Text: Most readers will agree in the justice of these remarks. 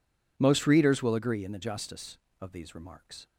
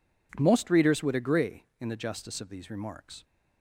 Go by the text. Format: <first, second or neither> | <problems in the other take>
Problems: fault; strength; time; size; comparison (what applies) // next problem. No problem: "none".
first | says "would" for "will"; at 1.0 s